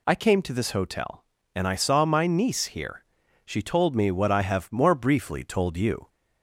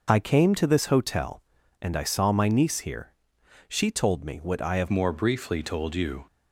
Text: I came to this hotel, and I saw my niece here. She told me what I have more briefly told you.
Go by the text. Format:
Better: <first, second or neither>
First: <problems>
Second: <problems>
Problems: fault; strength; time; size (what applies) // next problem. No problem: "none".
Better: first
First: none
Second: changes voice at "more"; from 4.8 s on; 1.4 s long